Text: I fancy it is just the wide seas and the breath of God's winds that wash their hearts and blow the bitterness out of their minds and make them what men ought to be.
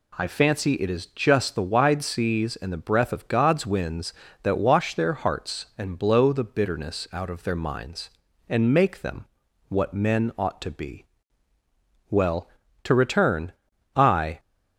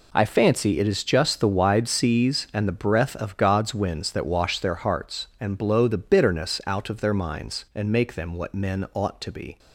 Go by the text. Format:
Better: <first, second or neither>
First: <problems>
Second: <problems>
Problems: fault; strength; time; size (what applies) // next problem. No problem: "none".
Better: second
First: pauses between "them" and "what"; at 9.2 s; 0.44 s long // goes on to say "Well to return I"; strong; from 12.1 s on; 2.2 s long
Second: none